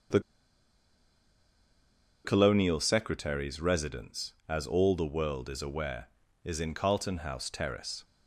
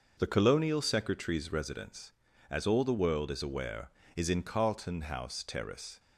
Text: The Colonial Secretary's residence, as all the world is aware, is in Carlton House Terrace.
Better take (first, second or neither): second